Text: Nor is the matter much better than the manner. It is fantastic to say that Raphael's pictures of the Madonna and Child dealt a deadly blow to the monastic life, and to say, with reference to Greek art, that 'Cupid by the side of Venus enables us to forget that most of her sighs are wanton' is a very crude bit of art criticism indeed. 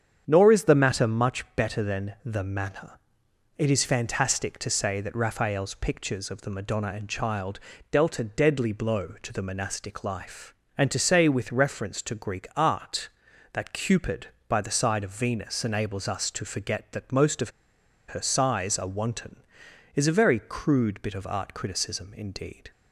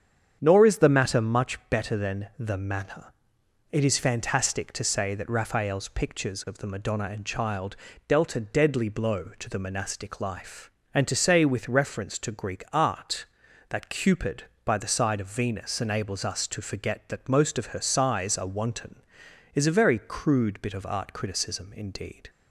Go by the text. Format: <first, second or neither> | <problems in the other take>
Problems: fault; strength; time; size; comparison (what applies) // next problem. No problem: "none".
second | starts louder than the rest; strong; until 1.2 s; 8 dB; strong in the second // pauses between "Child" and "dealt"; slight; at 7.5 s; 0.32 s long; slight in the second // pauses between "of" and "her"; noticeable; at 17.5 s; 0.57 s long